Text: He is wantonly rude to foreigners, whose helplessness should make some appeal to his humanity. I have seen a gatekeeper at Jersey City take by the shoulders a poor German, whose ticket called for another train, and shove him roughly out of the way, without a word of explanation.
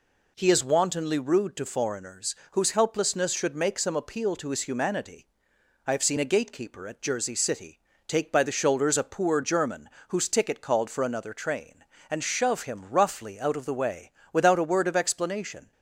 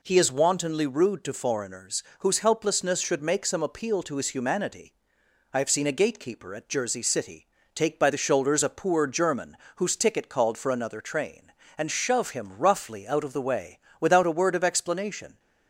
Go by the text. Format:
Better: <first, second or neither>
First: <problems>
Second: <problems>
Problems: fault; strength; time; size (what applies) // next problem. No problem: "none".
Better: neither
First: pauses between "City" and "take"; slight; at 7.7 s; 0.28 s long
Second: pauses between "City" and "take"; slight; at 7.4 s; 0.28 s long